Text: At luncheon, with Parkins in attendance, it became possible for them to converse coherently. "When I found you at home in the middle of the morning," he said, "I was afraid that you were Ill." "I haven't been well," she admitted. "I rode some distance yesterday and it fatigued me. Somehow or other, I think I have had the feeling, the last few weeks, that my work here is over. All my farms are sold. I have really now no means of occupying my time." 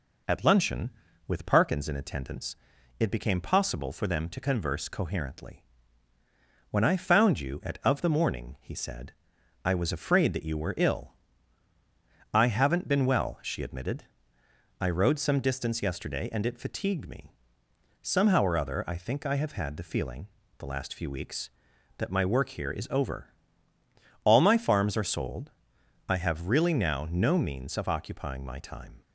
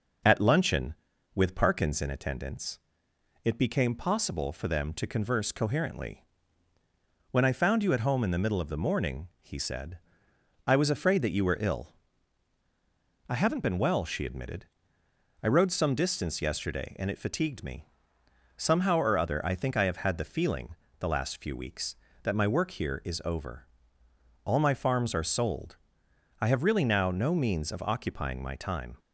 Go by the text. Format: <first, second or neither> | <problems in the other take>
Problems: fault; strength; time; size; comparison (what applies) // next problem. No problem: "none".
second | skips "home in the middle"; at 7.8 s